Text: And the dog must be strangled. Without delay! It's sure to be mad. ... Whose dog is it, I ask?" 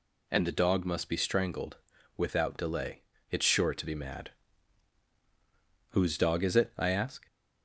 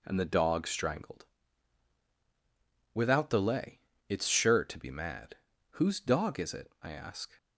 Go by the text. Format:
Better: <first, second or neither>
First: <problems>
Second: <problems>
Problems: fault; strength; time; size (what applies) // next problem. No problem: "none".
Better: first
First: none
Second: skips "must be"; at 0.6 s